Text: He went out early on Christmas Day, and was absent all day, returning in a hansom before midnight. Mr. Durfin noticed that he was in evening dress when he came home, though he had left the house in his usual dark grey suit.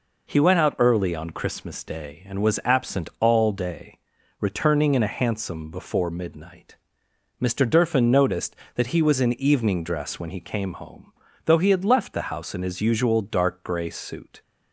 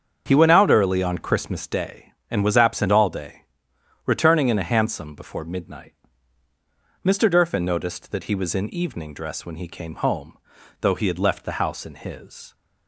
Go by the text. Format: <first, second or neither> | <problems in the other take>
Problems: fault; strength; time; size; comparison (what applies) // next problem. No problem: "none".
first | starts louder than the rest; until 1.2 s; 7 dB // stops before "usual dark grey suit"; at 12.5 s